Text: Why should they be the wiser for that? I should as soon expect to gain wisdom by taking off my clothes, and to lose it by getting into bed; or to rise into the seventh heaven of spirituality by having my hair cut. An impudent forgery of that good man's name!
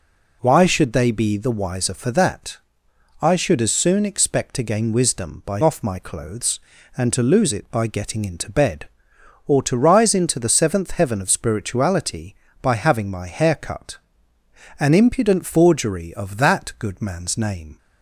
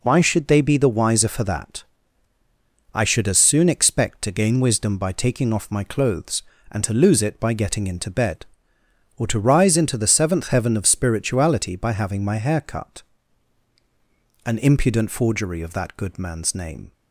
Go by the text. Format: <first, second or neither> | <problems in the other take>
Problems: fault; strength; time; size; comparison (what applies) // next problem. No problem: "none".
second | skips "taking"; at 5.6 s